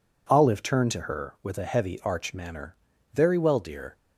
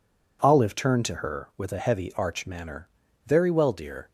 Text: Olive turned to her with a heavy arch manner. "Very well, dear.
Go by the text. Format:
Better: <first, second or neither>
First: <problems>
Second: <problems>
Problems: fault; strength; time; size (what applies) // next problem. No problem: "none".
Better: neither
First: none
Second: none